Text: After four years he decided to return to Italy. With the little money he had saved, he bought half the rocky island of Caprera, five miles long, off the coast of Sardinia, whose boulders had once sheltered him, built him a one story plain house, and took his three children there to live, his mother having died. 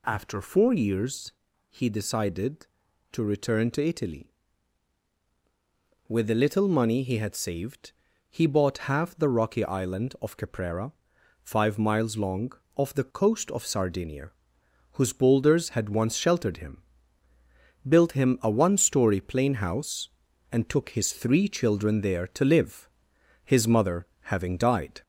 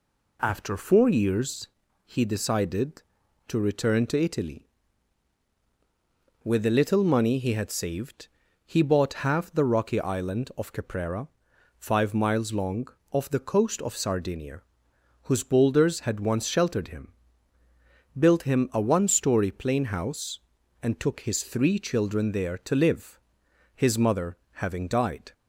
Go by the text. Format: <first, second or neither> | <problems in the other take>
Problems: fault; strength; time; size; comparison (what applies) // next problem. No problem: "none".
second | gets louder; slight; throughout; 2 dB // pauses between "years" and "he"; at 1.3 s; 0.40 s long; also in the second // pauses between "mother" and "having"; slight; at 24.0 s; 0.16 s long; slight in the second